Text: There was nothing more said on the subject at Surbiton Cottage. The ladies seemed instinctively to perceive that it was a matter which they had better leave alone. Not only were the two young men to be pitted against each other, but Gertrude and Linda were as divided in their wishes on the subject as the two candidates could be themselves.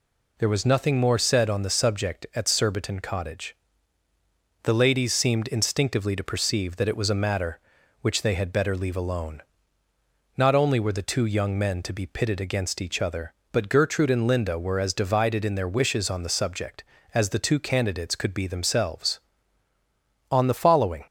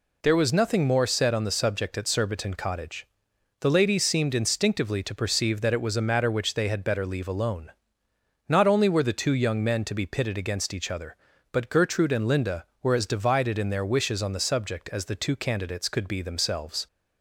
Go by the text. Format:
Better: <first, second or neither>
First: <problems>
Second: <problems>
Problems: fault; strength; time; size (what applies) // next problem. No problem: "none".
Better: second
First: goes on to say "On the following"; noticeable; from 20.3 s on; 0.74 s long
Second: none